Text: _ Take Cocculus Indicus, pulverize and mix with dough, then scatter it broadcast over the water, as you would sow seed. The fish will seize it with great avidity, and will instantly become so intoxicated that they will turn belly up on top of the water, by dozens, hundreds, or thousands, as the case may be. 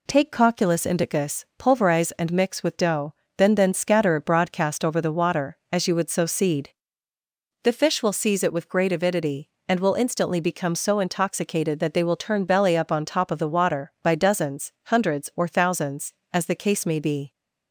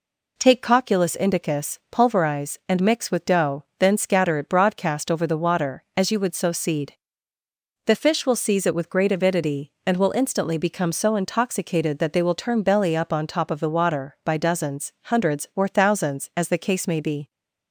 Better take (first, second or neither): second